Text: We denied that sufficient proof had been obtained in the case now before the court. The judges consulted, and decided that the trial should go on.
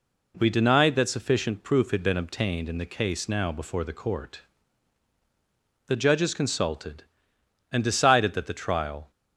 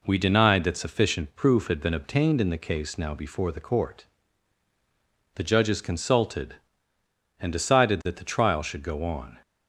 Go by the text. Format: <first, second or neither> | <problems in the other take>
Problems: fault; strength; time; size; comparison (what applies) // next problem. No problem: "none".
second | stops before "should go on"; at 9.1 s